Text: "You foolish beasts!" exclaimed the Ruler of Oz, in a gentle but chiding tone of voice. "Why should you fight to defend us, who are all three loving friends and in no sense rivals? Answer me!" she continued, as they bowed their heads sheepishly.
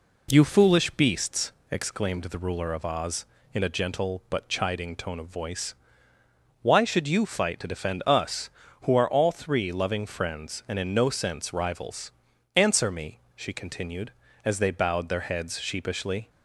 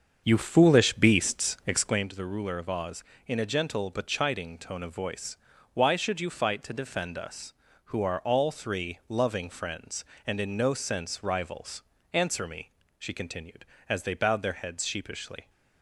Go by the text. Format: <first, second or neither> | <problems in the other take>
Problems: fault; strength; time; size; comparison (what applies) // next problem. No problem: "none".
first | starts louder than the rest; until 2.1 s; 7 dB